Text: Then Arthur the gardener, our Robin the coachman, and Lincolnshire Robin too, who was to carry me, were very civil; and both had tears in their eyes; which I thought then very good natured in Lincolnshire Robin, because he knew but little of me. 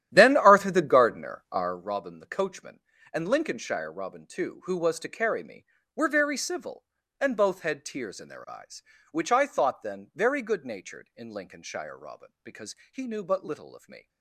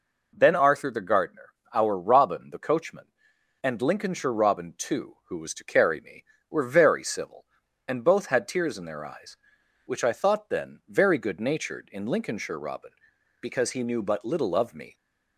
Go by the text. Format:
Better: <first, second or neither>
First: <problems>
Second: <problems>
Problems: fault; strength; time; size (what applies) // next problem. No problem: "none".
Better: second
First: starts louder than the rest; strong; until 1.8 s; 11.5 dB // pauses between "because" and "he"; slight; at 12.7 s; 0.16 s long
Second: none